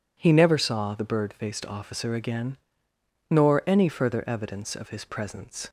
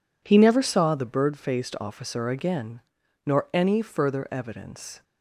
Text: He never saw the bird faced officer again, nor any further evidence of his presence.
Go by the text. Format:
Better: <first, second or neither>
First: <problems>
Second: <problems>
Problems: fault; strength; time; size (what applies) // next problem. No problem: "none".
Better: first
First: none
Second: stops before "of his presence"; at 5.0 s